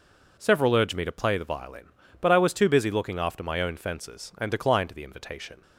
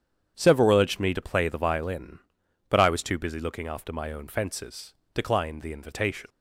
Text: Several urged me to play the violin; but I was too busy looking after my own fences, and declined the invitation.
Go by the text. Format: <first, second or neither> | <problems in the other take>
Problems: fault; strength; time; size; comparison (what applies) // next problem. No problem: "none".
first | starts louder than the rest; strong; until 1.3 s; 8.5 dB // skips "and"; at 5.0 s